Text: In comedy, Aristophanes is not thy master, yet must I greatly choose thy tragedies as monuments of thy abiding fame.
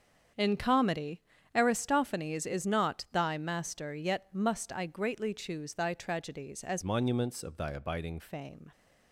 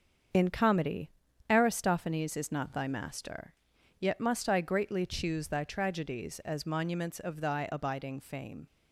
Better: second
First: starts louder than the rest; strong; until 1.6 s; 7.5 dB // changes voice from "monuments" to "abiding"; from 6.8 to 8.1 s; 1.3 s long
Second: starts louder than the rest; until 1.7 s; 7 dB

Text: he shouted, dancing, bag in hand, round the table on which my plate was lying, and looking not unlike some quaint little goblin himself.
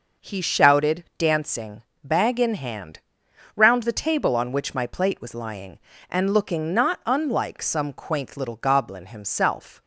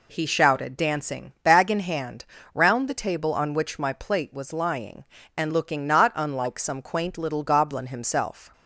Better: neither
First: none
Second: none

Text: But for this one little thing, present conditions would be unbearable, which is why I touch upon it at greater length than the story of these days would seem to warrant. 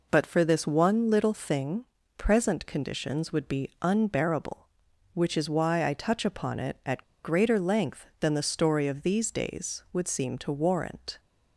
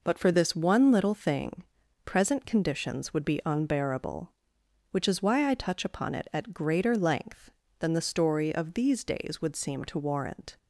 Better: second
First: pauses between "at" and "greater"; slight; at 7.0 s; 0.18 s long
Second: none

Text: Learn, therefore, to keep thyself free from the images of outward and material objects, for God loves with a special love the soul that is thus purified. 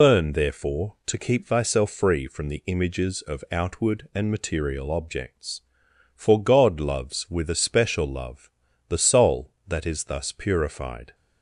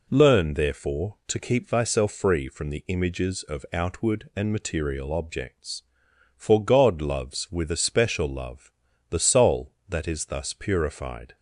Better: second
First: loses the start of "Learn"; at 0.0 s; 120 ms // pauses between "love" and "the"; at 8.4 s; 0.40 s long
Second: pauses between "love" and "the"; at 8.6 s; 0.40 s long

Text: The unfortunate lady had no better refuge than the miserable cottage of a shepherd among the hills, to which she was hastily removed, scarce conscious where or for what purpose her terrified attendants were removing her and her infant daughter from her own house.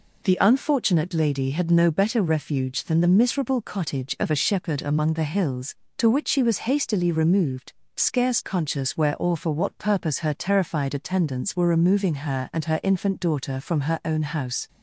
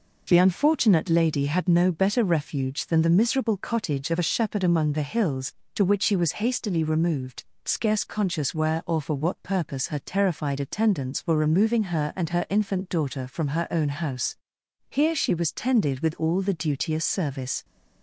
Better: first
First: none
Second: goes on to say "Here she was tended with all the duteous service"; strong; from 14.8 s on; 2.7 s long

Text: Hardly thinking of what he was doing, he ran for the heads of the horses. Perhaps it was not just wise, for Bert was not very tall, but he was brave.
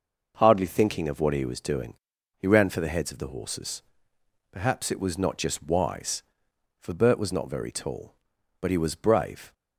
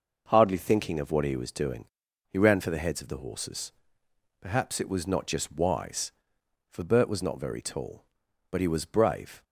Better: neither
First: none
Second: none

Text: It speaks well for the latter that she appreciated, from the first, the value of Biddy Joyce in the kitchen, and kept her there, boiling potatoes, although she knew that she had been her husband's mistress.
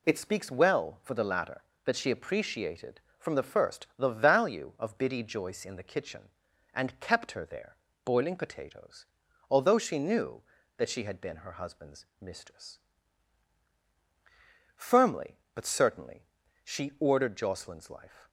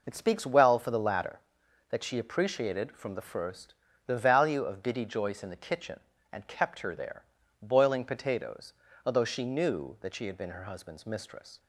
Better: second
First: pauses between "husband's" and "mistress"; slight; at 12.0 s; 0.16 s long // goes on to say "Firmly but certainly she ordered Jocelyn's life"; strong; from 14.7 s on; 3.5 s long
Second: none

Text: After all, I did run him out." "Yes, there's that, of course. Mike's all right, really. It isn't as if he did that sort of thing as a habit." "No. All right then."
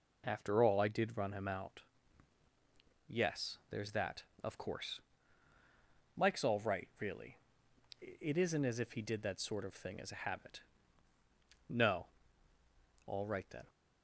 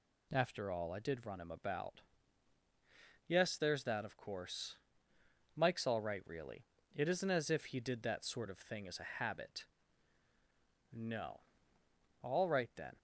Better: first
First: none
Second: says "about" for "out"; at 1.5 s

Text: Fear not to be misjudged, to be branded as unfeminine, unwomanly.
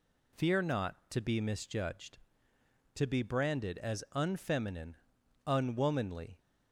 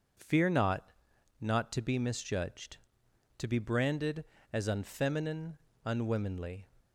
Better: first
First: none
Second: says "not" twice; at 1.3 s

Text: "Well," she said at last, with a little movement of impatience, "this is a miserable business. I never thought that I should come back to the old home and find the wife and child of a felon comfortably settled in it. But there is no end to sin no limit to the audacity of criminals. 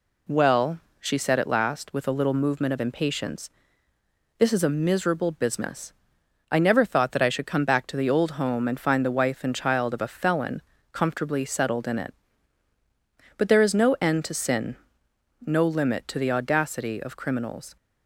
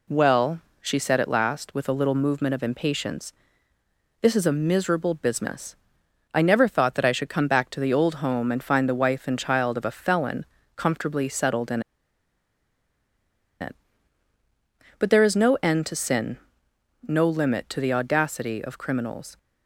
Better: first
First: pauses between "felon" and "comfortably"; slight; at 10.6 s; 0.30 s long // pauses between "sin" and "no"; noticeable; at 14.7 s; 0.70 s long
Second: pauses between "felon" and "comfortably"; slight; at 10.4 s; 0.30 s long // pauses between "in" and "it"; strong; at 11.8 s; 1.7 s long // pauses between "sin" and "no"; noticeable; at 16.3 s; 0.70 s long

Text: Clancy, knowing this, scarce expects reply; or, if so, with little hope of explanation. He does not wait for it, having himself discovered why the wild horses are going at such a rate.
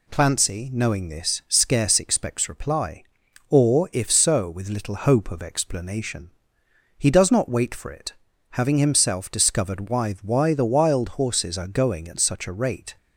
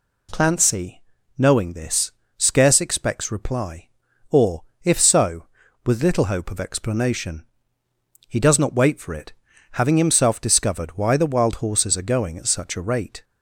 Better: second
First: says "why" twice; at 10.2 s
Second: none

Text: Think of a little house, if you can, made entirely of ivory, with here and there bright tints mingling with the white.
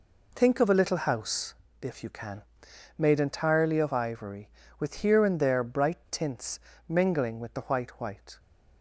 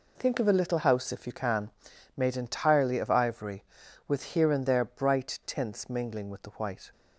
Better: second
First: pauses between "tints" and "mingling"; slight; at 6.5 s; 0.30 s long // says "white" twice; at 8.0 s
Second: none

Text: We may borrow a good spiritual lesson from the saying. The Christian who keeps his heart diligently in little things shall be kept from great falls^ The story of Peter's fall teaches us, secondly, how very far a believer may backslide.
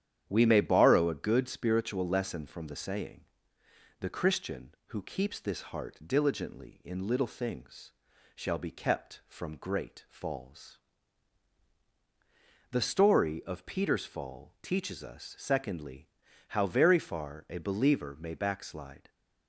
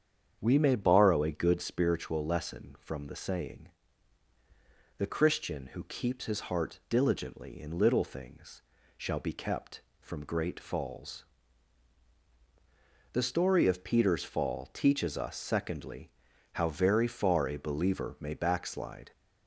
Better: second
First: starts louder than the rest; strong; until 1.2 s; 9.5 dB // says "this" for "his"; at 5.3 s // pauses between "things" and "shall"; at 7.9 s; 0.42 s long // pauses between "falls" and "The"; strong; at 10.7 s; 1.9 s long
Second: starts louder than the rest; strong; until 1.4 s; 8 dB // pauses between "things" and "shall"; slight; at 8.6 s; 0.34 s long // pauses between "falls" and "The"; strong; at 11.2 s; 1.8 s long

